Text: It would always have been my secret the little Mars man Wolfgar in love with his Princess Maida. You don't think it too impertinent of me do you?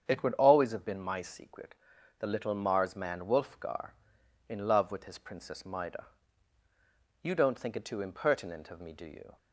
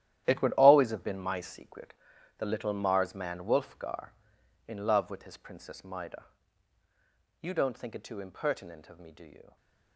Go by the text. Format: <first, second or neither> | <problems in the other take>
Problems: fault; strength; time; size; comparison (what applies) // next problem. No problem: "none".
first | gets quieter; strong; throughout; 13.5 dB // starts louder than the rest; strong; until 1.2 s; 11.5 dB; strong in the first // pauses between "secret" and "the"; at 1.9 s; 0.44 s long; also in the first